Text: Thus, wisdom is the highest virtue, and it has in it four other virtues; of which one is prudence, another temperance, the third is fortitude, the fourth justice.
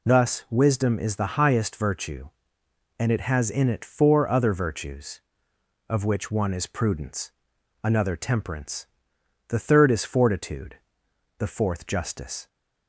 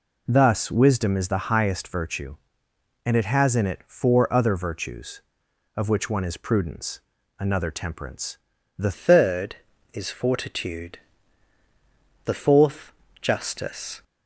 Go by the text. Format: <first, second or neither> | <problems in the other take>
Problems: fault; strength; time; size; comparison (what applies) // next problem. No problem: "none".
first | changes voice at "third"; from 8.9 s on; 5.1 s long // pauses between "fourth" and "justice"; slight; at 12.9 s; 0.26 s long